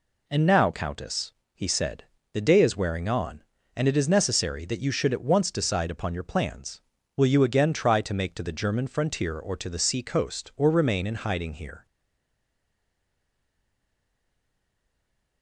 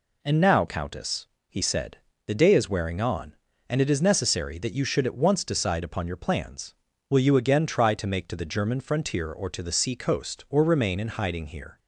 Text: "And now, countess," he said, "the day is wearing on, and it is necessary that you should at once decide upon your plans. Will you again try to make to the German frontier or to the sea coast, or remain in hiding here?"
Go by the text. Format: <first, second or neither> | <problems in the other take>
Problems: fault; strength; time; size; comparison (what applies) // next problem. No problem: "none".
second | stays silent after the last word; strong; from 11.8 s on; 3.6 s long